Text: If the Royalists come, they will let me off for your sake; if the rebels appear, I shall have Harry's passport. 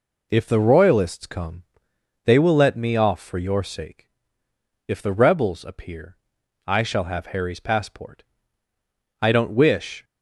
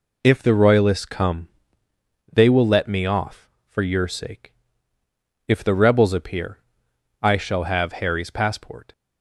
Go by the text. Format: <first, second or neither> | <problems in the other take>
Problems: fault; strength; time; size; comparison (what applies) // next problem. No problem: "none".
second | goes on to say "I don't wish"; noticeable; from 9.1 s on; 0.84 s long